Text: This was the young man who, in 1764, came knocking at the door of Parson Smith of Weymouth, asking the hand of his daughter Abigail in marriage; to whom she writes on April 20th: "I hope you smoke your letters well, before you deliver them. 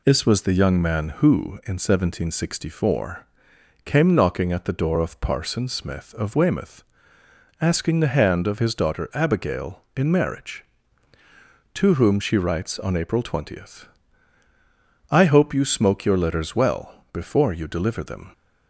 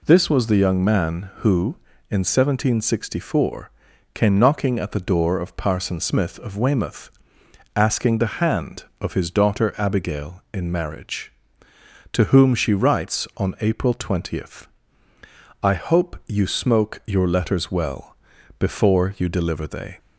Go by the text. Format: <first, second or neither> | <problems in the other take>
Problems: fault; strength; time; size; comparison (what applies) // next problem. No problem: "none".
first | says "they" for "them"; at 19.6 s